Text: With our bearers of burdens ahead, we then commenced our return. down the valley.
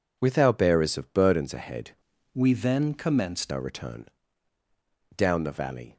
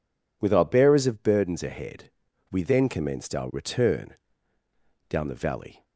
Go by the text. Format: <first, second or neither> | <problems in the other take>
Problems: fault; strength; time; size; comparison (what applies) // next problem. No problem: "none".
second | changes voice from "we" to "commenced"; from 2.3 to 3.5 s; 1.2 s long